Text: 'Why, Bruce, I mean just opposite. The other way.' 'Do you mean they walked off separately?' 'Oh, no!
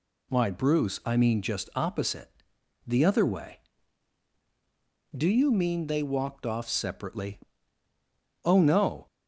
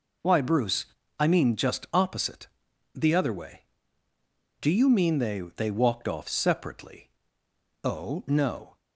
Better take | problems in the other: first | says "they" twice; at 5.5 s

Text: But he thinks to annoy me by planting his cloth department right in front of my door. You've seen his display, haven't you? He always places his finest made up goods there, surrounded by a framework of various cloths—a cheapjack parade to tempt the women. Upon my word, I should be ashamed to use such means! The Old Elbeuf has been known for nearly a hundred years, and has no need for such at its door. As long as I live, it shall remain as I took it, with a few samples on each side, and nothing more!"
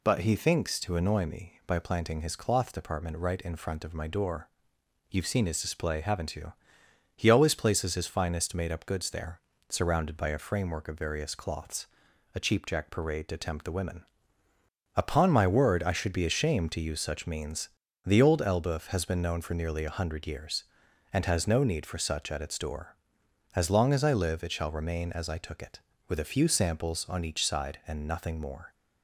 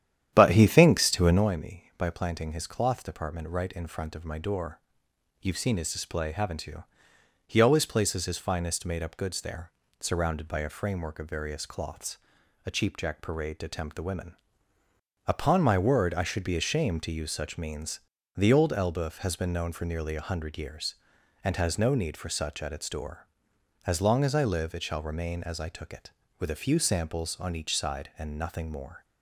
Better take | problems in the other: first | starts louder than the rest; strong; until 1.5 s; 10.5 dB

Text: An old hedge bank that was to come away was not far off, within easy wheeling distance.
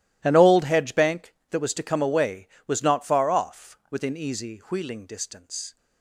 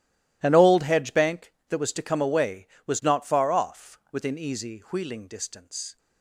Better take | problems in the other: neither | none

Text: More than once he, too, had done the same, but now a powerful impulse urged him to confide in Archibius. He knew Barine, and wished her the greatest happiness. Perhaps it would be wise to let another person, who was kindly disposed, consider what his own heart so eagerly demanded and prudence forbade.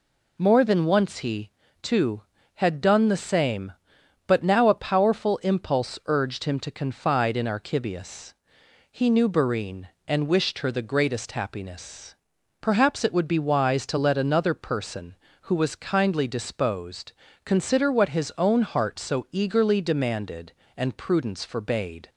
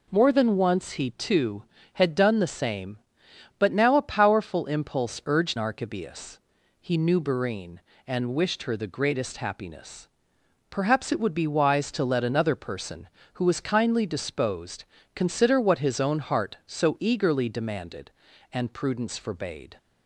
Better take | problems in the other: first | skips "him to confide in"; at 5.5 s

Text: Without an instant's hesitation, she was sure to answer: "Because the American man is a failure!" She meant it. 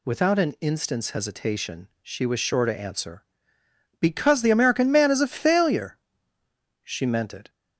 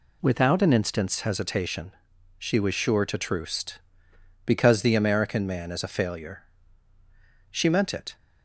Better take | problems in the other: first | says "troost" for "answer"; at 3.1 s

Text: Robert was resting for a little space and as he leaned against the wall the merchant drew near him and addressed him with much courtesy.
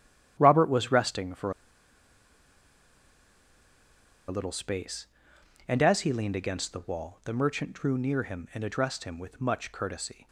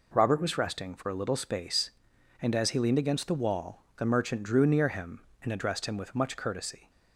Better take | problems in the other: second | starts louder than the rest; strong; until 1.3 s; 11 dB // pauses between "for" and "a"; strong; at 1.5 s; 2.7 s long

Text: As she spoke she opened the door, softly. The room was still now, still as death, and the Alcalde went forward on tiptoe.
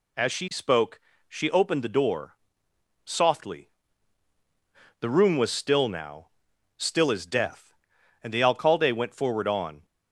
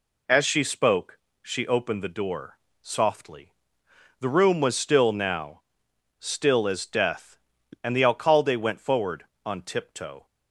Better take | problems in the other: second | pauses between "spoke" and "she"; slight; at 0.9 s; 0.28 s long; slight in the second // stops before "tiptoe"; at 9.8 s

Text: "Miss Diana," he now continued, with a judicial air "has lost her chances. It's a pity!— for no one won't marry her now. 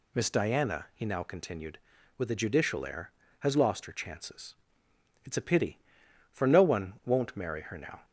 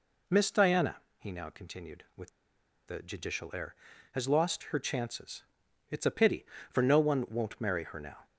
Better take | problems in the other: first | pauses between "with" and "a"; noticeable; at 2.2 s; 0.59 s long

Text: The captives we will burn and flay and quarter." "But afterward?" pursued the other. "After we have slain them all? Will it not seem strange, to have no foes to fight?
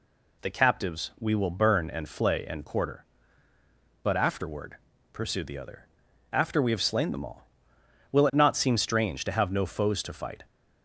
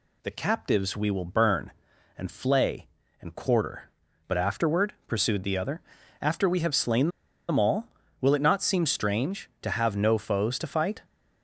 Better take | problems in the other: first | pauses between "slain" and "them"; at 7.0 s; 0.40 s long

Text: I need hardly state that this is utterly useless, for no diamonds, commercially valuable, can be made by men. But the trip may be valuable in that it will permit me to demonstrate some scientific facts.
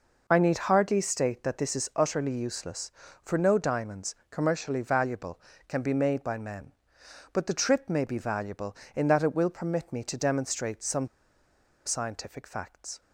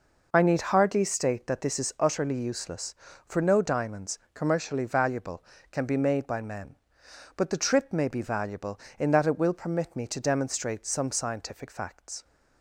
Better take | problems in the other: second | pauses between "some" and "scientific"; noticeable; at 11.0 s; 0.78 s long

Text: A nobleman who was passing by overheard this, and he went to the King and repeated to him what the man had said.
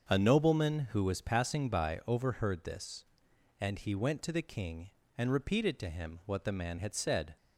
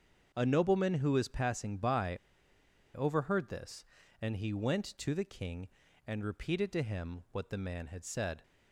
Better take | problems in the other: first | starts louder than the rest; until 1.3 s; 7 dB; also in the first // pauses between "by" and "overheard"; noticeable; at 2.1 s; 0.78 s long

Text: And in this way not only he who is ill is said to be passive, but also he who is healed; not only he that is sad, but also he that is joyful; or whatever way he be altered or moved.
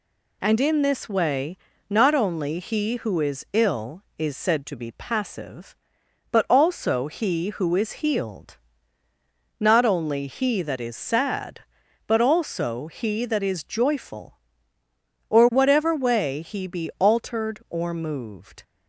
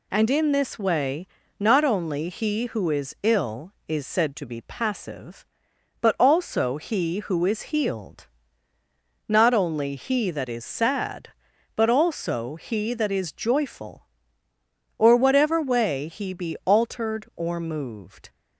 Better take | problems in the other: neither | pauses between "way" and "not"; slight; the same in both

